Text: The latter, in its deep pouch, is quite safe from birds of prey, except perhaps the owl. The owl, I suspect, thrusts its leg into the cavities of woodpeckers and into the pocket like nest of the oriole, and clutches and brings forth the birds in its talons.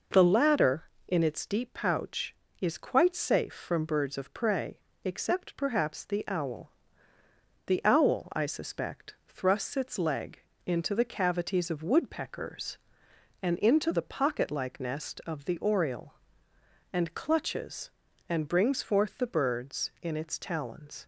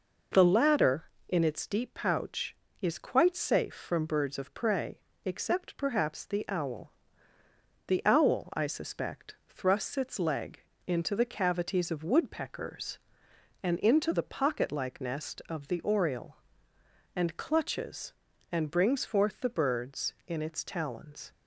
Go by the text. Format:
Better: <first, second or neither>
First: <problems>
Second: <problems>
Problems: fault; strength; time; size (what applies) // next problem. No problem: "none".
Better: neither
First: pauses between "leg" and "into"; slight; at 10.3 s; 0.26 s long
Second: pauses between "leg" and "into"; slight; at 10.6 s; 0.26 s long